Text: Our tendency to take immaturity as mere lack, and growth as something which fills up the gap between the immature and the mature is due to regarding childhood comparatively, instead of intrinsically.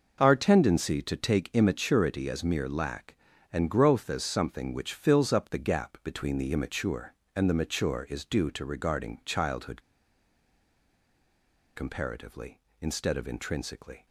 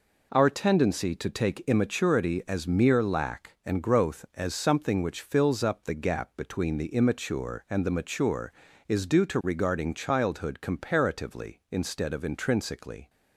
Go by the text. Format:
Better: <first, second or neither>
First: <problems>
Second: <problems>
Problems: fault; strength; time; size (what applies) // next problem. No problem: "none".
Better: second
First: pauses between "childhood" and "comparatively"; strong; at 9.7 s; 1.9 s long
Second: none